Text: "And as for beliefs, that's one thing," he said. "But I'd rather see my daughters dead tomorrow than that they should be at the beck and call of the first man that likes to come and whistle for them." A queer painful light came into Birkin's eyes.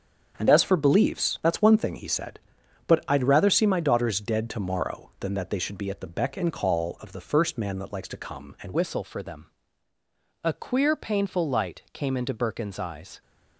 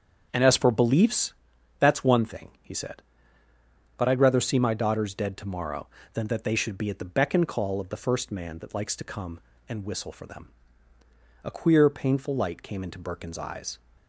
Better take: second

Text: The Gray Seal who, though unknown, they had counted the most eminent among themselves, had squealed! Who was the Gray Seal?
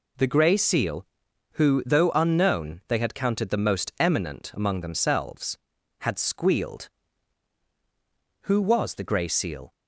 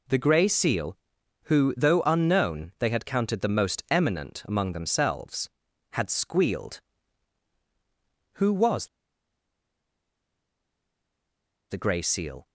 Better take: first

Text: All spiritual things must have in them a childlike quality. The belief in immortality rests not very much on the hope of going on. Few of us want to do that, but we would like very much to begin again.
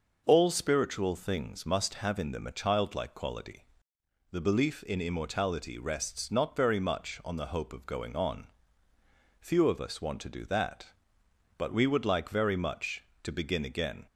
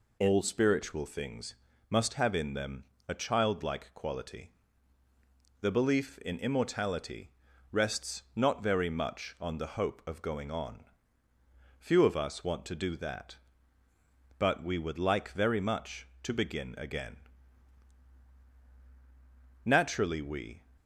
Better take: first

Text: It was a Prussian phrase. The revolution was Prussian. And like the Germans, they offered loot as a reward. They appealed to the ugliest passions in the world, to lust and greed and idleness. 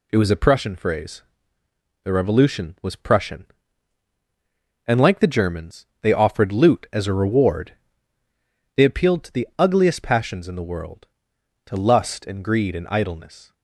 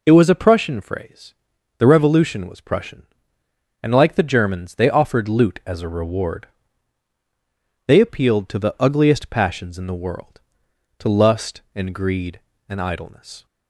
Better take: neither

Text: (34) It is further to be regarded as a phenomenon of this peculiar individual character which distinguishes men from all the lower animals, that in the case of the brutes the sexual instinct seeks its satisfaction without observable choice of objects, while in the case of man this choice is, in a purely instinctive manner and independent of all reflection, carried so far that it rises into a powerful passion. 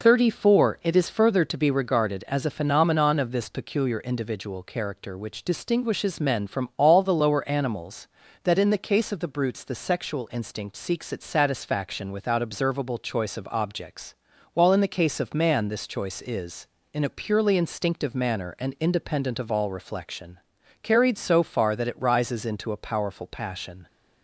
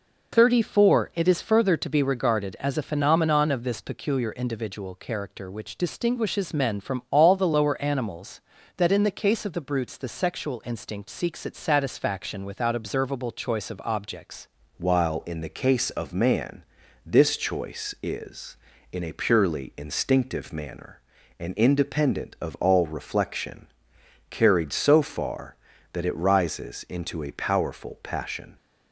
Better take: first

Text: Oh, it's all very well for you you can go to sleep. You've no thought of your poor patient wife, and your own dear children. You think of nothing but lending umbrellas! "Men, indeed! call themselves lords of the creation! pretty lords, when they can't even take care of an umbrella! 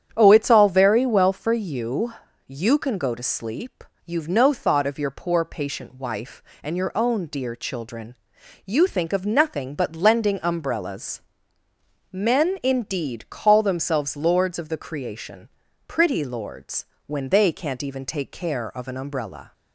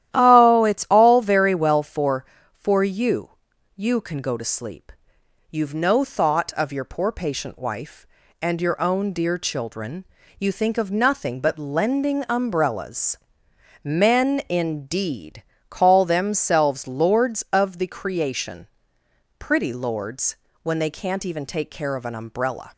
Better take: first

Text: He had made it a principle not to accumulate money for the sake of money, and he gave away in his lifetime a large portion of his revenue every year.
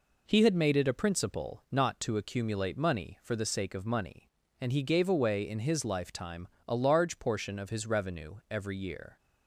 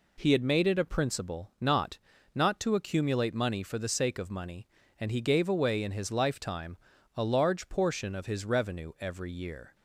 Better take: first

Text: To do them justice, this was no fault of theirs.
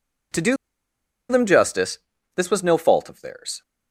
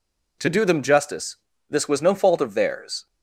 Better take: second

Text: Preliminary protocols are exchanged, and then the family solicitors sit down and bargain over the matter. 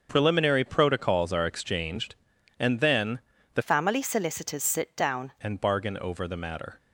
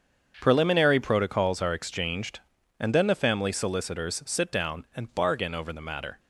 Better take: second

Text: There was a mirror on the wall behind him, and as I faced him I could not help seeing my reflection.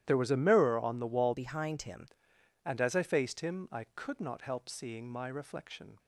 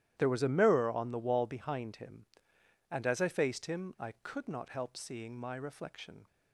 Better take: second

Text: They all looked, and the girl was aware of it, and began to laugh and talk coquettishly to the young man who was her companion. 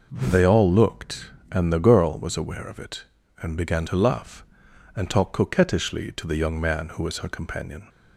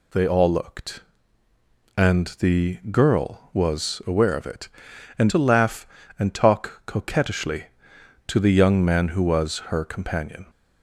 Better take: first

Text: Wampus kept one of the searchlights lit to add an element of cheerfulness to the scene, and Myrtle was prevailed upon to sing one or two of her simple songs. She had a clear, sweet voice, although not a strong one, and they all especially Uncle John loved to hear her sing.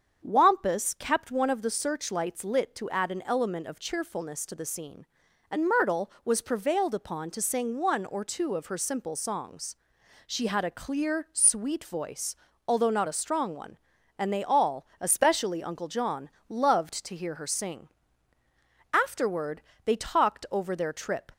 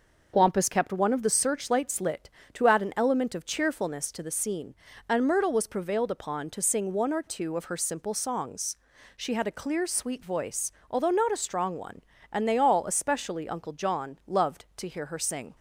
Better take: second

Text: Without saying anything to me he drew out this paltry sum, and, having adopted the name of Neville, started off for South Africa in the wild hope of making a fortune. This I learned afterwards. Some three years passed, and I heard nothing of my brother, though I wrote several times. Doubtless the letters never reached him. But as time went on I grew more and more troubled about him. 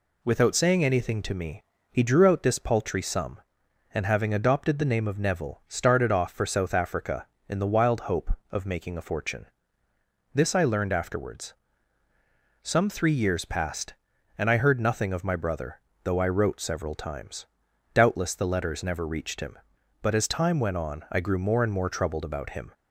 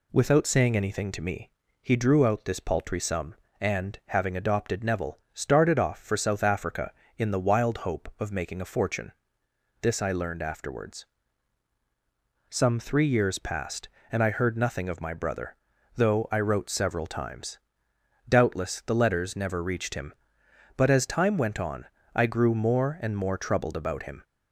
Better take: first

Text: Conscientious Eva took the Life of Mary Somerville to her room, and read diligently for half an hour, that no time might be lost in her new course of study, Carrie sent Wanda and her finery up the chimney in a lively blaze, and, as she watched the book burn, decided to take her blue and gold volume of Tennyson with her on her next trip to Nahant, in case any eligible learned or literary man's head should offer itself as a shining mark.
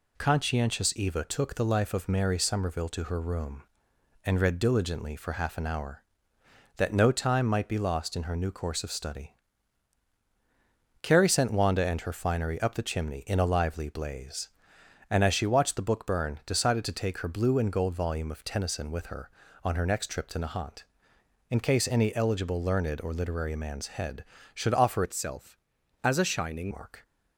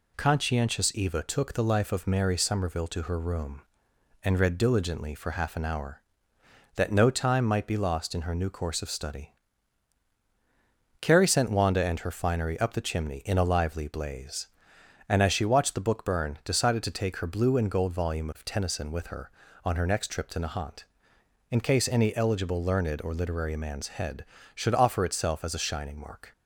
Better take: second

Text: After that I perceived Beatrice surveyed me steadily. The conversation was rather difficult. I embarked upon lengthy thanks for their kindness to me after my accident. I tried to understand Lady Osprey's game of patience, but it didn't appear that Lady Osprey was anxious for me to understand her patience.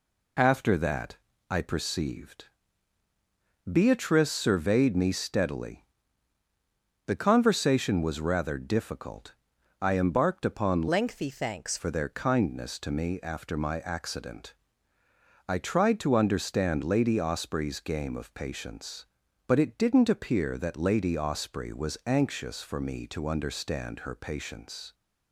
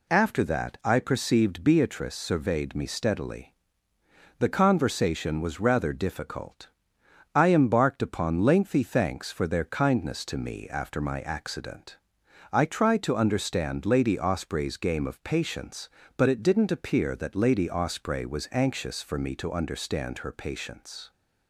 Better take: second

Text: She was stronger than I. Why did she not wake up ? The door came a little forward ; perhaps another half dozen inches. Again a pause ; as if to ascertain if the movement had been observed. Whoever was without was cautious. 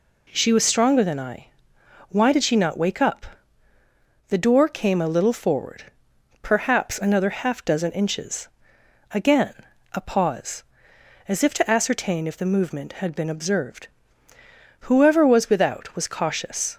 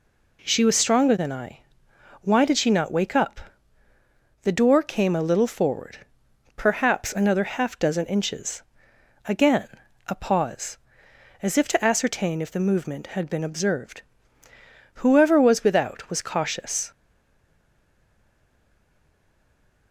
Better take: first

